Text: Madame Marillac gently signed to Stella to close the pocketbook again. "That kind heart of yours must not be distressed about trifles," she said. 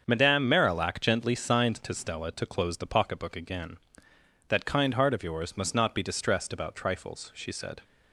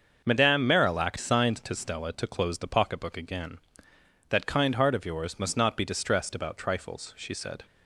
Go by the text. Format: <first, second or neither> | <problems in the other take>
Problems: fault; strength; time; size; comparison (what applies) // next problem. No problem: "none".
first | starts louder than the rest; until 1.2 s; 6.5 dB; also in the first // skips "gently"; at 1.1 s